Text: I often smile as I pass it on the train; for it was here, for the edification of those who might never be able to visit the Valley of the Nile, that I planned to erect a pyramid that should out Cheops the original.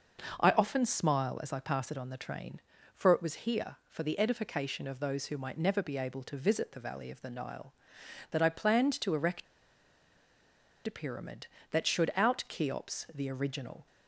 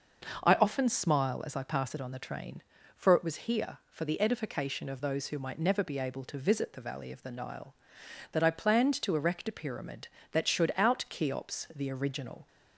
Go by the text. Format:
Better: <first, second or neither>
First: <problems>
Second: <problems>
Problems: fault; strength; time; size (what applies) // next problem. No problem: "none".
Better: second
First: pauses between "erect" and "a"; strong; at 9.4 s; 1.4 s long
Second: none